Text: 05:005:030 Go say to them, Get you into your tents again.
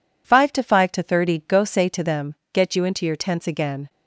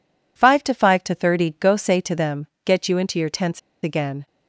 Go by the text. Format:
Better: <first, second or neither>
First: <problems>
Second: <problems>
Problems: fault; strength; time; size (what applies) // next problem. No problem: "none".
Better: first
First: none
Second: pauses between "tents" and "again"; slight; at 3.5 s; 0.24 s long